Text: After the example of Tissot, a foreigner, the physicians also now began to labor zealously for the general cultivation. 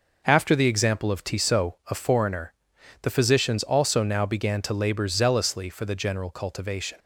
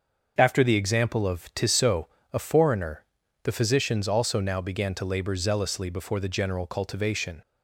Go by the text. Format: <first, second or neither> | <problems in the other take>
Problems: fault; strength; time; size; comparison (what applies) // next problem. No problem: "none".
first | starts louder than the rest; until 1.3 s; 6.5 dB // says "before" for "for"; at 5.8 s